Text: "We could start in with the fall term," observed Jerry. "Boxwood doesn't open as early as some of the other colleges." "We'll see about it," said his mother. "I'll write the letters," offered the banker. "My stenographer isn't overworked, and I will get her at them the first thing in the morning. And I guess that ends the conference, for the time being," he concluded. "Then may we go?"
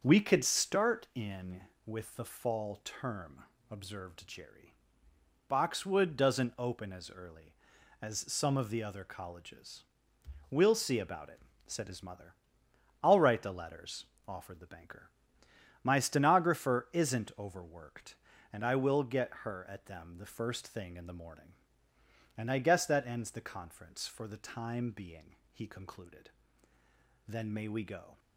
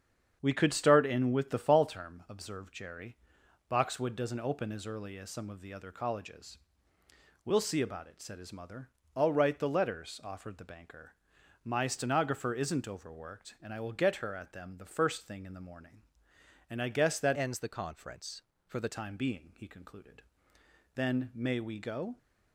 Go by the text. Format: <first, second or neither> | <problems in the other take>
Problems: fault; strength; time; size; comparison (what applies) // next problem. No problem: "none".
first | starts louder than the rest; strong; until 1.4 s; 8 dB; also in the first // changes voice from "ends" to "the"; from 17.3 to 18.8 s; 1.5 s long